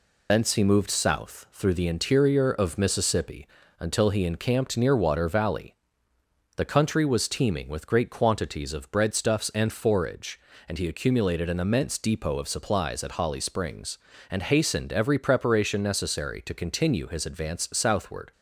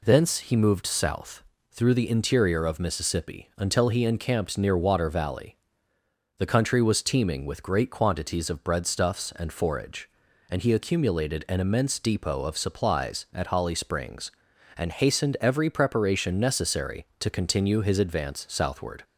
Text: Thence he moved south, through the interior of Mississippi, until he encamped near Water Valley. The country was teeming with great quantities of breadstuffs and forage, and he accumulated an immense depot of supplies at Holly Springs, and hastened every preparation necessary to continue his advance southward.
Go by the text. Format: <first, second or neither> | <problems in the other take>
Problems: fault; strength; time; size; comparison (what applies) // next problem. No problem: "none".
second | loses the start of "Thence"; at 0.2 s; 65 ms